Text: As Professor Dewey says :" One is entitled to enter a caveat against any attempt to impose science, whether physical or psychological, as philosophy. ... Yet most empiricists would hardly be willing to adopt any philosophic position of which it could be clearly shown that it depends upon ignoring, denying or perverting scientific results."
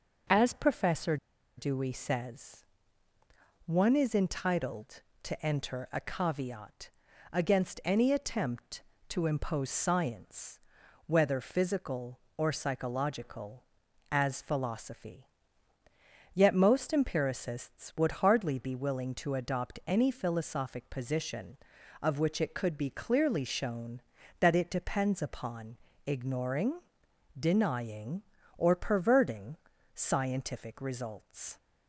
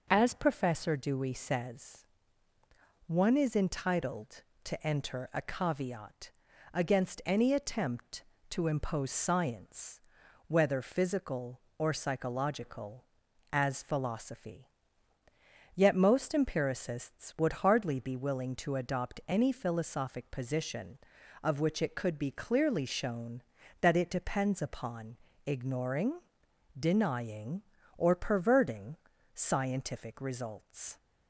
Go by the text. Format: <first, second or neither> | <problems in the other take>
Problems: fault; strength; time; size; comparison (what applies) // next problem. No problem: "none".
second | pauses between "Professor" and "Dewey"; at 1.1 s; 0.41 s long // pauses between "caveat" and "against"; at 6.8 s; 0.42 s long; also in the second // pauses between "upon" and "ignoring"; slight; at 25.7 s; 0.30 s long; slight in the second // pauses between "perverting" and "scientific"; at 29.5 s; 0.40 s long; also in the second